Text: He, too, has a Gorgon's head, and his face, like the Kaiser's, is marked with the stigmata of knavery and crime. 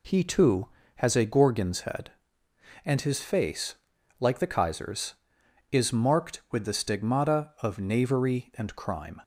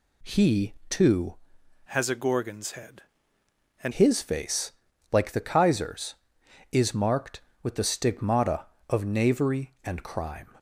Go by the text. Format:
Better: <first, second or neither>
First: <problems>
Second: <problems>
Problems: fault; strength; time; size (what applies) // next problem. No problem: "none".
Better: first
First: none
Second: changes voice from "has" to "and"; from 1.8 to 3.9 s; 2.1 s long